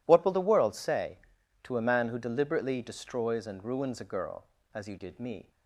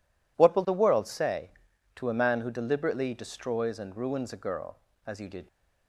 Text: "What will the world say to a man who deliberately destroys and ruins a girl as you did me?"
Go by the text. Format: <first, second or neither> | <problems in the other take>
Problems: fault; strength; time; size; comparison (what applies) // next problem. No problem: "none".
first | stops before "me"; at 5.4 s